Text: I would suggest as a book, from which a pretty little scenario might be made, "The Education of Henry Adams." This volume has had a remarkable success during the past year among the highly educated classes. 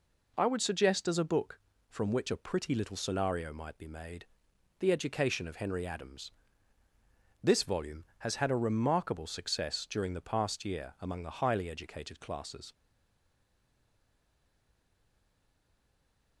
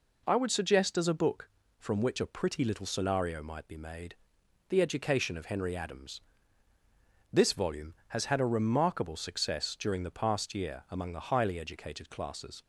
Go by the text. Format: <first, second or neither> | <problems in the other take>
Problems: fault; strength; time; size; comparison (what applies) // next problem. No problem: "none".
second | stays silent after the last word; strong; from 12.7 s on; 3.7 s long